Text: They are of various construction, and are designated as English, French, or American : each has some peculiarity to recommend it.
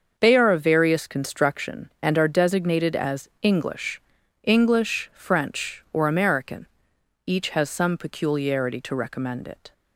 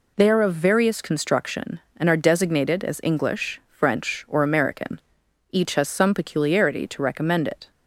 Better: second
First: starts louder than the rest; until 1.1 s; 6.5 dB // says "English" twice; at 4.4 s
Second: none

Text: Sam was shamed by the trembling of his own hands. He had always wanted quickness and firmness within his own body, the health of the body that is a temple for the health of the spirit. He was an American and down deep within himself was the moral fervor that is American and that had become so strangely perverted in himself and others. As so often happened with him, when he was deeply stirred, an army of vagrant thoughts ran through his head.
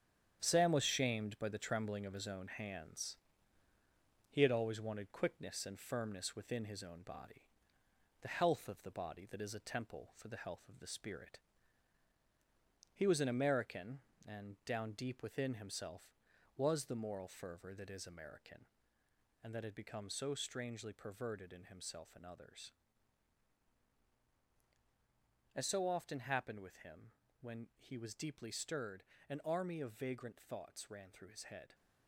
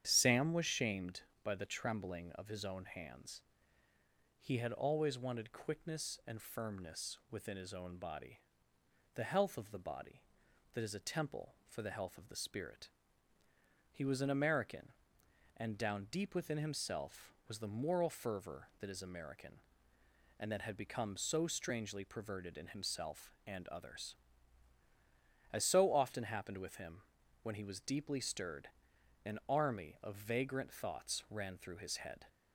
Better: second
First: gets quieter; throughout; 7 dB // starts louder than the rest; strong; until 1.4 s; 8.5 dB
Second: starts louder than the rest; strong; until 1.0 s; 9 dB

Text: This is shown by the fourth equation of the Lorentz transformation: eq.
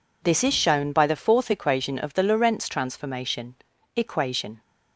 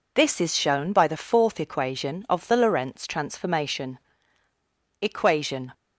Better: neither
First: none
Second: none

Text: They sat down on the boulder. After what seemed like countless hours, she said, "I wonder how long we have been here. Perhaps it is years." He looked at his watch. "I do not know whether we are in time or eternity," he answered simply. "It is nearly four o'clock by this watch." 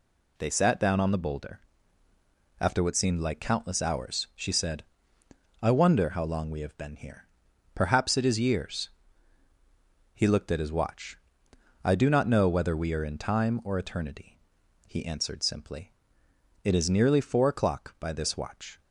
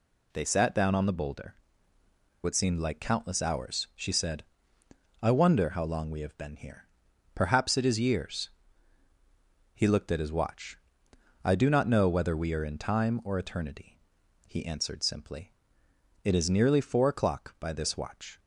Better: first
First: none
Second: skips "After"; at 1.9 s

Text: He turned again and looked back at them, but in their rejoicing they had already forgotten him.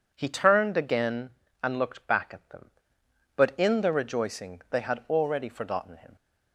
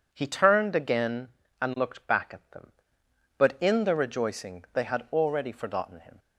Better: neither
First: none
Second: none

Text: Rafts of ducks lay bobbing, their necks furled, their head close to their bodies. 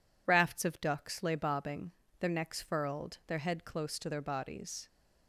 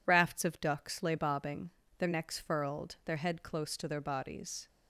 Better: neither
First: none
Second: none

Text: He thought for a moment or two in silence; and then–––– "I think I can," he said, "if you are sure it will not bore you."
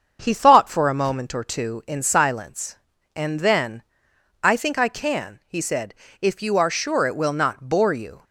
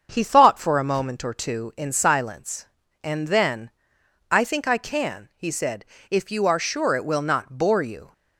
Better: neither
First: starts louder than the rest; until 1.2 s; 7 dB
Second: starts louder than the rest; until 1.1 s; 7 dB

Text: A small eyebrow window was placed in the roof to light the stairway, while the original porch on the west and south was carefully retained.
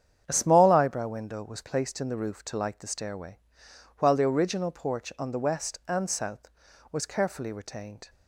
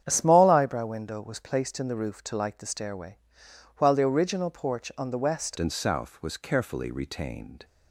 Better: first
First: starts louder than the rest; strong; until 1.2 s; 8.5 dB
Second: starts louder than the rest; strong; until 1.0 s; 9 dB // changes voice at "and"; from 5.5 s on; 2.1 s long

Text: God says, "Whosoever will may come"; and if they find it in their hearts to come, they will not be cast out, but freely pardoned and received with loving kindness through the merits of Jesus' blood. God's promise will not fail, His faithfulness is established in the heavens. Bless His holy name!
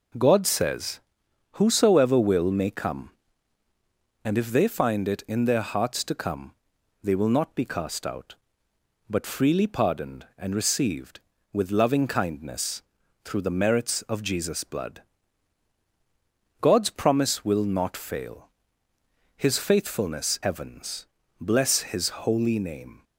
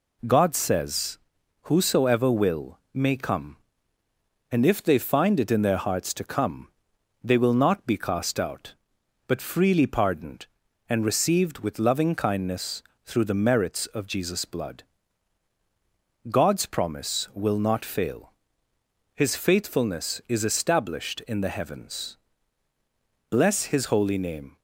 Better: second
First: pauses between "kindness" and "through"; at 12.8 s; 0.44 s long // skips "is established in the"; at 20.4 s // pauses between "His" and "holy"; slight; at 22.0 s; 0.16 s long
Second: pauses between "kindness" and "through"; slight; at 12.8 s; 0.24 s long

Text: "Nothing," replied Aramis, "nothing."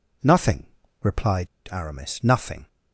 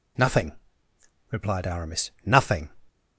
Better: second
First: pauses between "replied" and "Aramis"; slight; at 1.4 s; 0.24 s long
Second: none

